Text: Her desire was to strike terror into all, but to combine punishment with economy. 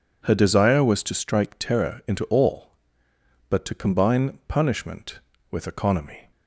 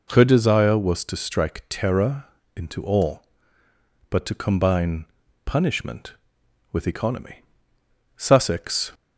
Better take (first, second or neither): first